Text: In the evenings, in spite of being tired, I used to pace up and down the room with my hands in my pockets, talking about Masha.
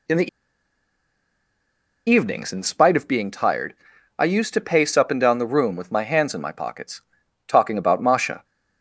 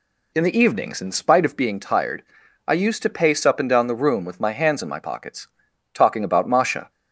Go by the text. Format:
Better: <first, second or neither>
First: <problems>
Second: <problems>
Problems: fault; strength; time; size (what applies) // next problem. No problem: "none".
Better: second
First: pauses between "the" and "evenings"; strong; at 0.2 s; 1.8 s long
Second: none